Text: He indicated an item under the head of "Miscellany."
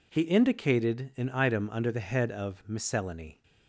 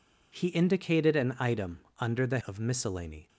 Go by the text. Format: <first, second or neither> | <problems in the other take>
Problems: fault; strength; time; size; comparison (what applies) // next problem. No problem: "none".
first | pauses between "item" and "under"; slight; at 1.7 s; 0.22 s long // skips "head"; at 2.4 s